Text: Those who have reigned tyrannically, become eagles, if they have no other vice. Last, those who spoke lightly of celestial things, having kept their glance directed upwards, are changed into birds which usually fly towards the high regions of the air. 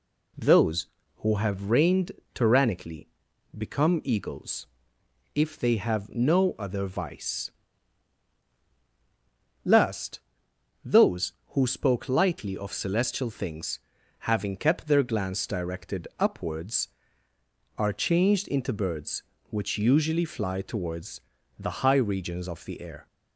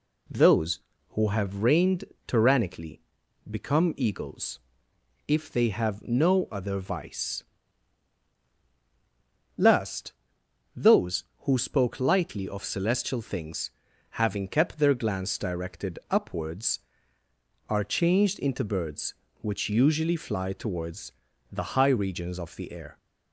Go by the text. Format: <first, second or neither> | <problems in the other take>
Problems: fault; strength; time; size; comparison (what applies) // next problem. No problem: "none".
neither | pauses between "reigned" and "tyrannically"; slight; the same in both // pauses between "towards" and "the"; the same in both